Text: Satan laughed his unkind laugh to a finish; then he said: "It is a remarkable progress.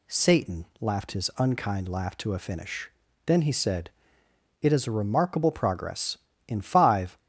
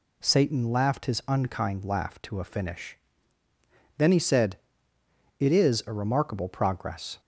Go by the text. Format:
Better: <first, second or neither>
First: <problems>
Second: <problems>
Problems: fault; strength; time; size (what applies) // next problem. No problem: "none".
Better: second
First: goes on to say "In five"; noticeable; from 6.4 s on; 0.72 s long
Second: none